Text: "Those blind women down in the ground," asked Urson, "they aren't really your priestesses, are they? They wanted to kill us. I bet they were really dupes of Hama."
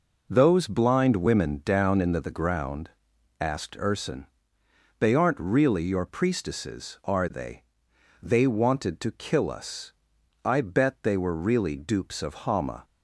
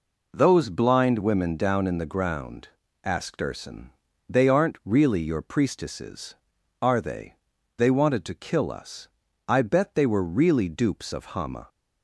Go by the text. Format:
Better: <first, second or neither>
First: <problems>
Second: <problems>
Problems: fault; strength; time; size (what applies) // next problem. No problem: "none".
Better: second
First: says "the" twice; at 2.1 s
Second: none